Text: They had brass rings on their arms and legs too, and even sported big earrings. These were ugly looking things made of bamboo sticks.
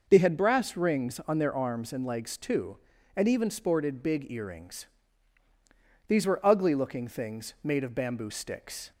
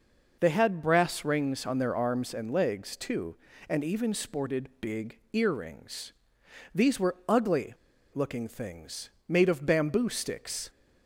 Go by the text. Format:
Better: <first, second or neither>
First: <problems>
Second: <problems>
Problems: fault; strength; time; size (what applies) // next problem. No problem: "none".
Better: first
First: none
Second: pauses between "ugly" and "looking"; at 7.7 s; 0.39 s long // pauses between "things" and "made"; slight; at 9.0 s; 0.18 s long